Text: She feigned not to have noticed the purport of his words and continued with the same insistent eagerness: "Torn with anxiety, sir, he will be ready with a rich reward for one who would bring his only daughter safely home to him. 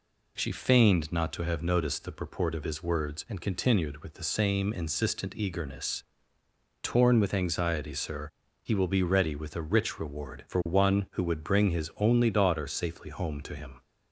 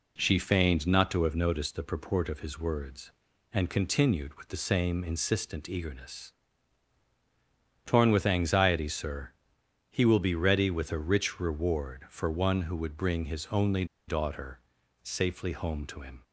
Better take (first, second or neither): first